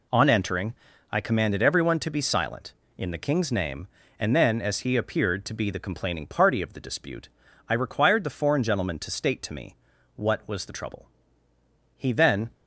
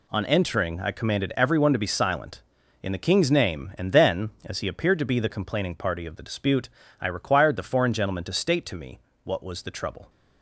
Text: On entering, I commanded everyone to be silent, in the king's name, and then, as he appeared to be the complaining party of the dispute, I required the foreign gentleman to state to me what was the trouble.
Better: second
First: pauses between "me" and "what"; at 9.7 s; 0.40 s long // goes on to say "He then"; from 11.9 s on; 0.54 s long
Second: pauses between "me" and "what"; slight; at 8.9 s; 0.24 s long

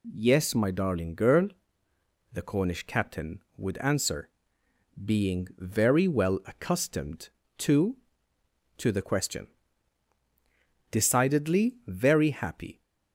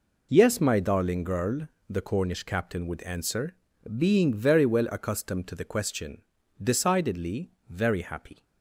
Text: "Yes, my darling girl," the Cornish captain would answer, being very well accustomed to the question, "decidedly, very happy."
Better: second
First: says "to" twice; at 8.7 s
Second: none

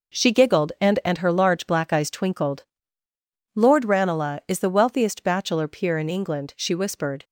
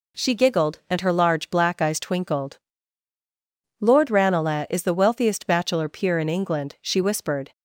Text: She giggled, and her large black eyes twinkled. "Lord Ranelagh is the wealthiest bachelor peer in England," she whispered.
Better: second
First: says "and" twice; at 1.0 s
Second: none

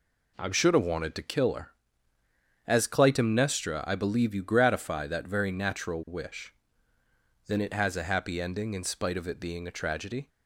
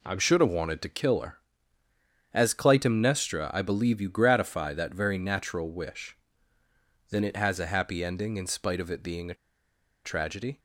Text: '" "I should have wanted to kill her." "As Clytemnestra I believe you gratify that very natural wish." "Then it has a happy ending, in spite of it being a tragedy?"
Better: first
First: none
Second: pauses between "a" and "tragedy"; noticeable; at 9.3 s; 0.69 s long

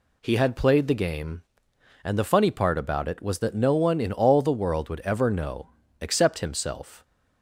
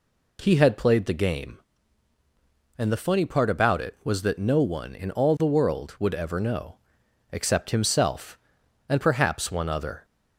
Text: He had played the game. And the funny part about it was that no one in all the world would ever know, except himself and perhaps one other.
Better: second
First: stops before "and perhaps one other"; at 7.0 s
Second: none

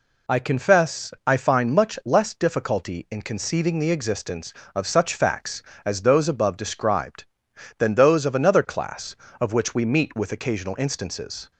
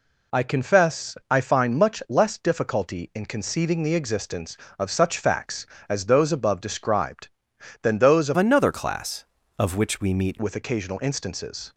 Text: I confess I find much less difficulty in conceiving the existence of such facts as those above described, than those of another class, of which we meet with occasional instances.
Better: first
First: pauses between "confess" and "I"; slight; at 1.1 s; 0.16 s long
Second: pauses between "confess" and "I"; slight; at 1.1 s; 0.16 s long // changes voice from "another" to "meet"; from 8.3 to 10.3 s; 2.0 s long

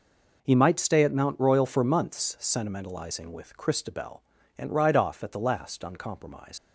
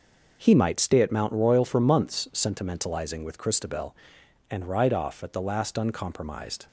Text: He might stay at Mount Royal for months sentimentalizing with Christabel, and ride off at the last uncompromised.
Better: second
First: leaves "uncompromised" unfinished; at 6.5 s; 120 ms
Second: none

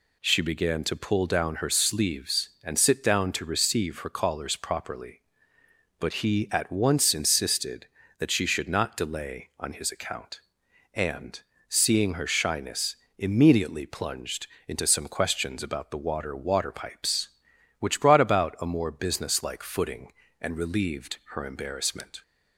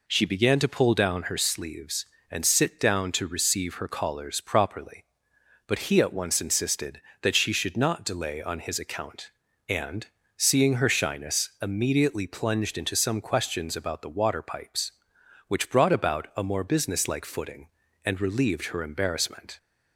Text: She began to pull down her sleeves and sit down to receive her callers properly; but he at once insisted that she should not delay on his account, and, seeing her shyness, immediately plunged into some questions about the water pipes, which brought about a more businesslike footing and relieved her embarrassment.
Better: second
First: pauses between "plunged" and "into"; slight; at 14.4 s; 0.20 s long // says "water" twice; at 16.3 s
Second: none

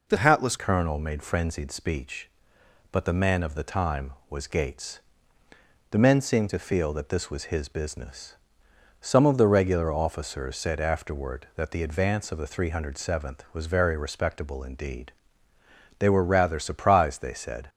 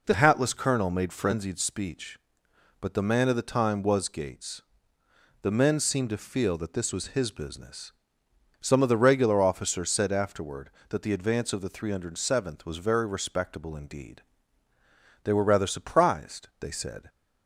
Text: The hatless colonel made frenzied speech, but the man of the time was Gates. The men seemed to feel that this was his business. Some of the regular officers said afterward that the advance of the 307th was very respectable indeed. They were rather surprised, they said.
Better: second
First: changes voice at "colonel"; from 0.5 s on; 17.1 s long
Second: none

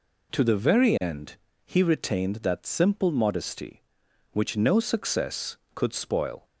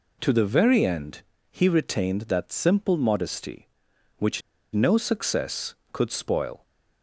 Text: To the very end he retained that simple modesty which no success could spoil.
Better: first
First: pauses between "end" and "he"; slight; at 1.3 s; 0.28 s long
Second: pauses between "end" and "he"; slight; at 1.2 s; 0.28 s long // pauses between "which" and "no"; slight; at 4.4 s; 0.33 s long

